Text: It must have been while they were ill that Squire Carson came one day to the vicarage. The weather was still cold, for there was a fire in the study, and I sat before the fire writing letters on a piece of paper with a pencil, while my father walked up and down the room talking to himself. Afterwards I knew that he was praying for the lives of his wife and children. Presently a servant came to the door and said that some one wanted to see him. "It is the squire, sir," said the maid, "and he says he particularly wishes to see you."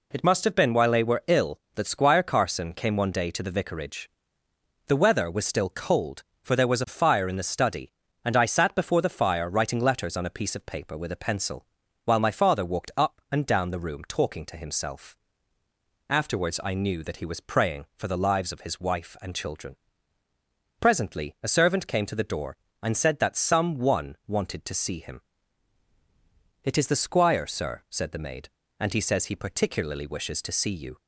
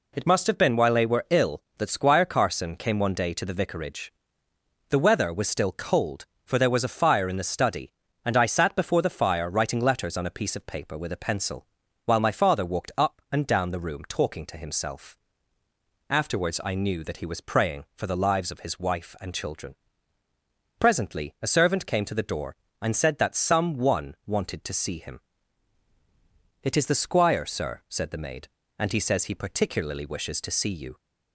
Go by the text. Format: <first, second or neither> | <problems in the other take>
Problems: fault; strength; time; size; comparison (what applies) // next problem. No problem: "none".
neither | none